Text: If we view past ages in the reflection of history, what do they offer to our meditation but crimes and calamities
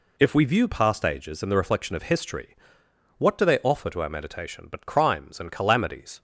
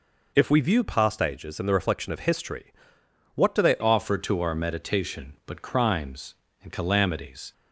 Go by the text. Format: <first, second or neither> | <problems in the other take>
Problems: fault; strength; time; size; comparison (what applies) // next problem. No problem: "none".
first | changes voice at "offer"; from 3.7 s on; 3.8 s long